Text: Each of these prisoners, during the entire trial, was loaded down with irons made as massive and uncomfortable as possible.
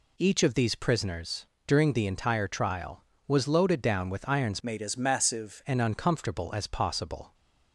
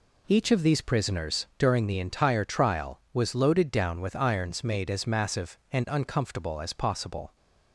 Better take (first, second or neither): second